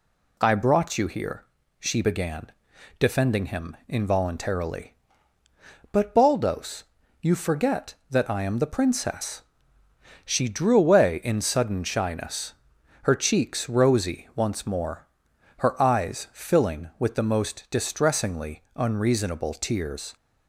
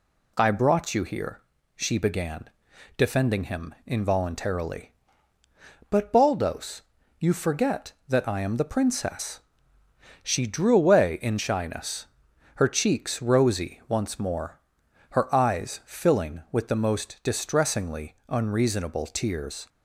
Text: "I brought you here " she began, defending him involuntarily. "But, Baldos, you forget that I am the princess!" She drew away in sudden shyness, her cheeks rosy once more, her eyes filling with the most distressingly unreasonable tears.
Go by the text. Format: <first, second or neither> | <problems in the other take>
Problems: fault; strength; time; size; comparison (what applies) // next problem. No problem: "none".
first | skips "sudden"; at 11.3 s